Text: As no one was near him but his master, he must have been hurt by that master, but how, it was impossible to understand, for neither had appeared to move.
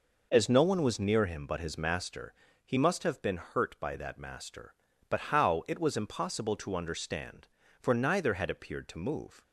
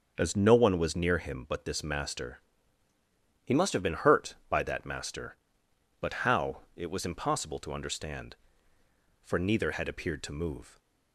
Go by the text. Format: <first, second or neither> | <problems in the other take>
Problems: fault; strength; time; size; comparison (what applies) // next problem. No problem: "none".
first | starts louder than the rest; until 1.1 s; 6.5 dB // says "this" for "his"; at 1.6 s